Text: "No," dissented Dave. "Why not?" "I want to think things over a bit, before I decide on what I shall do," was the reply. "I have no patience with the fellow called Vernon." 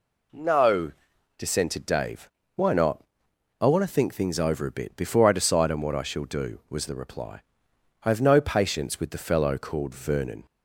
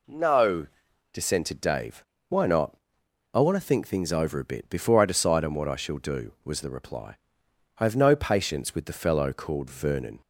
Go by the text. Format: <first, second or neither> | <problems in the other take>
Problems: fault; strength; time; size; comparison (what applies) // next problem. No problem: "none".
neither | none